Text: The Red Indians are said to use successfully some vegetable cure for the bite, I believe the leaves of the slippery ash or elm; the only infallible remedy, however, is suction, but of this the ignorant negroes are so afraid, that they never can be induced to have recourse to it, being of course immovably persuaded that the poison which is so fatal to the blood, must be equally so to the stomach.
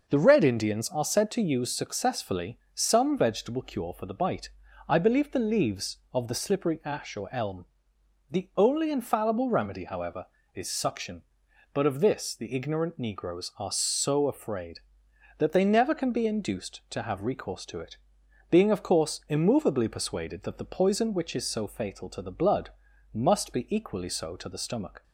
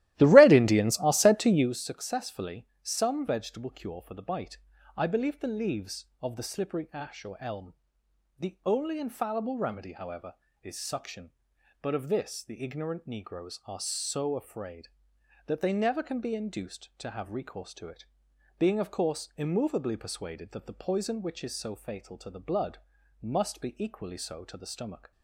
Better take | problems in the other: first | starts louder than the rest; strong; until 1.7 s; 15 dB

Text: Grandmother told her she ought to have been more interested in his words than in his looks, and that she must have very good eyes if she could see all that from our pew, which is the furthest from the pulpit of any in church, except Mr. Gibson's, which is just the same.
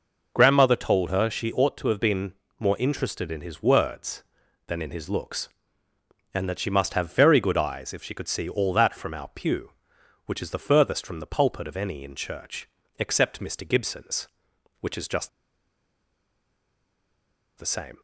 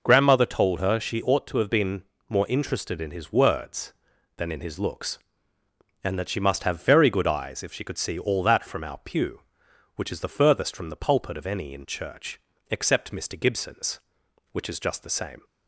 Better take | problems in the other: second | pauses between "been" and "more"; slight; at 2.3 s; 0.26 s long; slight in the second // pauses between "just" and "the"; strong; at 15.2 s; 2.2 s long

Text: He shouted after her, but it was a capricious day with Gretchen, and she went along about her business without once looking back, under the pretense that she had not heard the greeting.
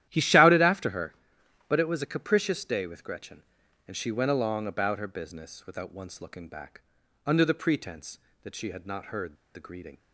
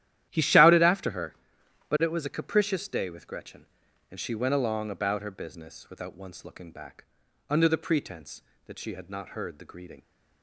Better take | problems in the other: second | starts louder than the rest; strong; until 1.0 s; 12.5 dB; strong in the second // pauses between "heard" and "the"; slight; at 9.3 s; 0.20 s long

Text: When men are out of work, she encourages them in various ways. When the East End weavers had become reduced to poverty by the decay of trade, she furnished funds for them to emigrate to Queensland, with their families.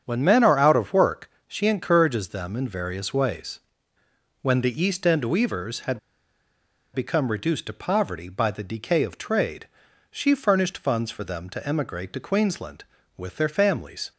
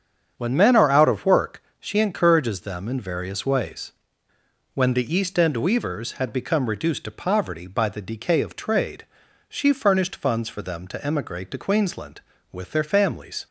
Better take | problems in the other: second | starts louder than the rest; strong; until 1.0 s; 8 dB; strong in the second // pauses between "had" and "become"; noticeable; at 5.9 s; 0.94 s long

